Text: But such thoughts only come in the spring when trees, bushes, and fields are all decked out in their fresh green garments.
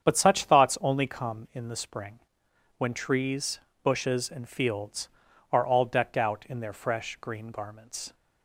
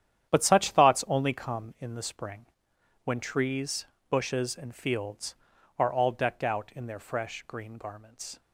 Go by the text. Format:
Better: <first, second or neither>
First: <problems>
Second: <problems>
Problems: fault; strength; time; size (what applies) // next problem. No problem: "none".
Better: first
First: starts louder than the rest; strong; until 1.0 s; 8 dB // pauses between "spring" and "when"; noticeable; at 2.2 s; 0.58 s long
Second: gets quieter; strong; throughout; 11 dB // starts louder than the rest; strong; until 1.3 s; 10 dB // pauses between "spring" and "when"; noticeable; at 2.4 s; 0.58 s long